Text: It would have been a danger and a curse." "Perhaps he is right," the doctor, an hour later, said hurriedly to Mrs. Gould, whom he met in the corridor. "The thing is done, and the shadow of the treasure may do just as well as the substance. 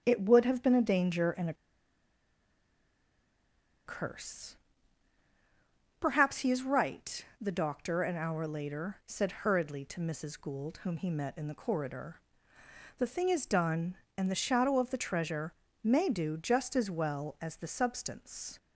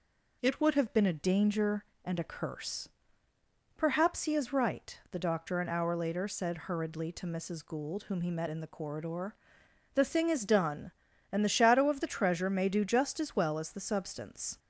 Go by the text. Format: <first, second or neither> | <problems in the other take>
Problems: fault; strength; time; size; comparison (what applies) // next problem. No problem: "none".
second | starts louder than the rest; strong; until 1.0 s; 9 dB // pauses between "a" and "curse"; strong; at 1.5 s; 2.3 s long // pauses between "treasure" and "may"; slight; at 15.5 s; 0.30 s long